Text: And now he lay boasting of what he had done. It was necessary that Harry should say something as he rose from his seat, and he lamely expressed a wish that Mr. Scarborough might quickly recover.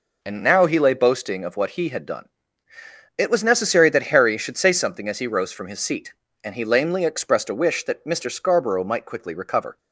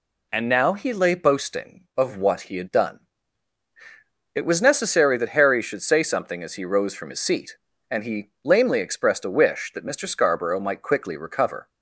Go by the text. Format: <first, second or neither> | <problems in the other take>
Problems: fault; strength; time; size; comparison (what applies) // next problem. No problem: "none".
neither | none